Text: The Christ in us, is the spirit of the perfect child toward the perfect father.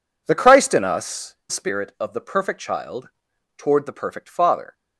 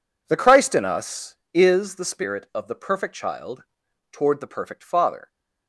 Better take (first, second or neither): second